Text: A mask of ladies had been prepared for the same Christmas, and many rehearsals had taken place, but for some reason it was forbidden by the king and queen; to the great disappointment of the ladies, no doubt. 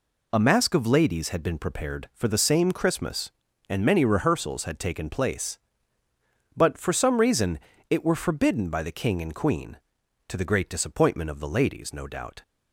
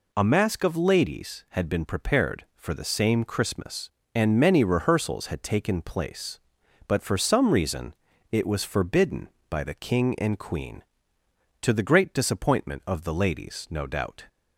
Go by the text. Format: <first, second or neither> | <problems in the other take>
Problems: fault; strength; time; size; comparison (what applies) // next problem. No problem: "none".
second | pauses between "reason" and "it"; slight; at 7.6 s; 0.30 s long; slight in the second // says "were" for "was"; at 8.0 s